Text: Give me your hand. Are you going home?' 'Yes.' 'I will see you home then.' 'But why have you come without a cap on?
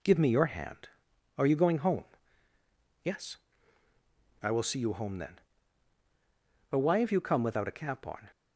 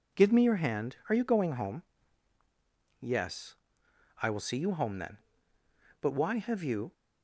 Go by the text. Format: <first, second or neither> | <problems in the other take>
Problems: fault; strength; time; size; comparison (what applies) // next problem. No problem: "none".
first | stops before "come without a cap on"; at 6.9 s